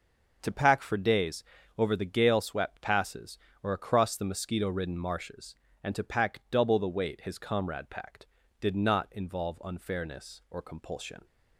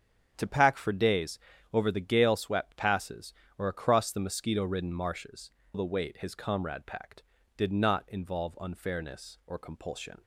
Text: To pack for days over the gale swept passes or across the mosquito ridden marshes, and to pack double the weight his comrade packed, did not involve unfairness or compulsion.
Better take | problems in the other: first | starts louder than the rest; strong; until 1.3 s; 8 dB // pauses between "days" and "over"; slight; at 1.3 s; 0.34 s long; slight in the first // skips "and to pack double"; at 5.6 s

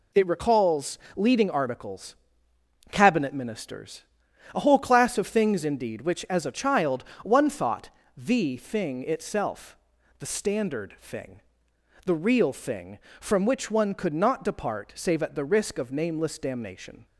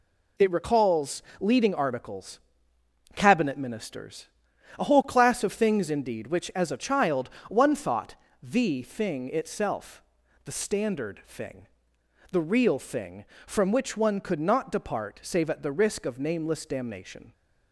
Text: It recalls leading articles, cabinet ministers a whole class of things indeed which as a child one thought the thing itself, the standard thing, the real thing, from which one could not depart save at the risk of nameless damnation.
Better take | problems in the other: neither | pauses between "recalls" and "leading"; slight; the same in both // pauses between "ministers" and "a"; noticeable; the same in both // pauses between "child" and "one"; slight; the same in both // pauses between "thought" and "the"; slight; the same in both

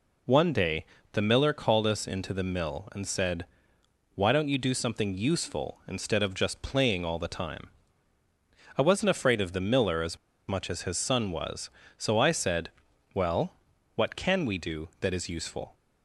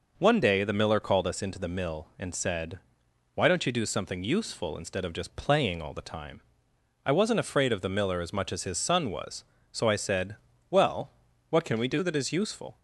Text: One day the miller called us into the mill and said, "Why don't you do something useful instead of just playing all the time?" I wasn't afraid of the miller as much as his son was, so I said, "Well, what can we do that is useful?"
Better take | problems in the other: second | pauses between "day" and "the"; slight; at 0.8 s; 0.28 s long // pauses between "as" and "much"; slight; at 10.1 s; 0.32 s long

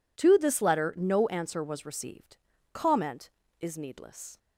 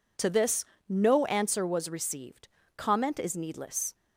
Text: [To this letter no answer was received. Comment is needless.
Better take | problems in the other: first | skips "letter"; at 0.7 s

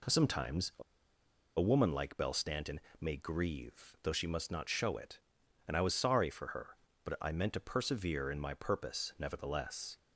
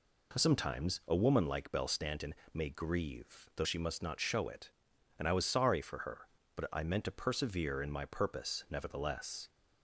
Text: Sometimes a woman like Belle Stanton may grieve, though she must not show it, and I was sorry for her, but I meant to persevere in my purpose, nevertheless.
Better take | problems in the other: second | pauses between "a" and "woman"; noticeable; at 0.8 s; 0.77 s long // pauses between "Stanton" and "may"; slight; at 2.7 s; 0.20 s long; slight in the second

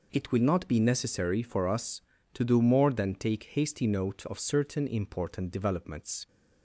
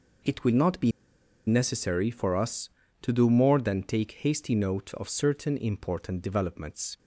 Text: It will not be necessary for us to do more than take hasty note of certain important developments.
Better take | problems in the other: first | pauses between "be" and "necessary"; noticeable; at 0.9 s; 0.56 s long

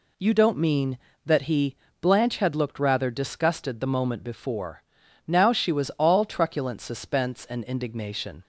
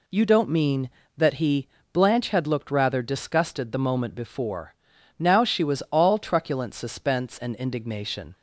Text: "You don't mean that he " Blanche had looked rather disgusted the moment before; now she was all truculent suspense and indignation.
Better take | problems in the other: neither | none

